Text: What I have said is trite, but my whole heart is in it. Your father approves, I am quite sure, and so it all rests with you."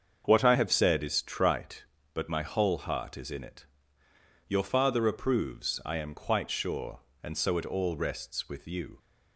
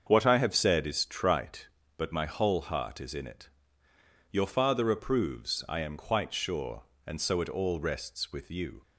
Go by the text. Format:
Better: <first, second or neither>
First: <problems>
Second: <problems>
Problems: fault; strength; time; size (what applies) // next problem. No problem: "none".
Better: neither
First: starts louder than the rest; until 1.2 s; 7 dB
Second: starts louder than the rest; until 1.0 s; 7 dB